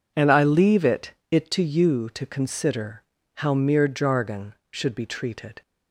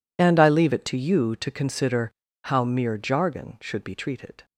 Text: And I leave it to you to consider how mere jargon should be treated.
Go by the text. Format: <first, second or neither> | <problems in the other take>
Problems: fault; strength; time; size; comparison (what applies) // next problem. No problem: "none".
second | says "it" twice; at 1.2 s // pauses between "consider" and "how"; slight; at 3.0 s; 0.34 s long; slight in the second